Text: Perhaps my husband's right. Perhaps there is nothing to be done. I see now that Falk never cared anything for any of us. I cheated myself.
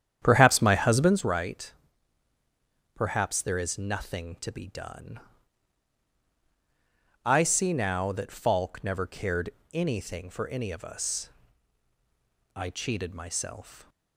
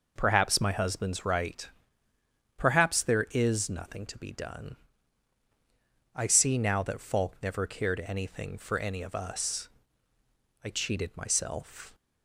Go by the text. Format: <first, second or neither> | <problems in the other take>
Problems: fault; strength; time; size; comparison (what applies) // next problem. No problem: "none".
second | starts louder than the rest; strong; until 1.4 s; 9.5 dB // pauses between "cared" and "anything"; slight; at 9.4 s; 0.24 s long